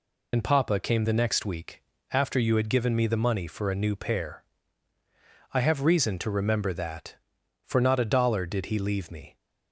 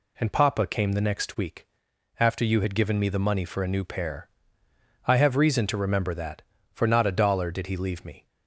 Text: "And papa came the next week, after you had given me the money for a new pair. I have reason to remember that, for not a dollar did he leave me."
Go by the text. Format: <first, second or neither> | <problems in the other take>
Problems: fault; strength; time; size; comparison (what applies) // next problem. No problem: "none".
second | loses the start of "And"; at 0.3 s; 50 ms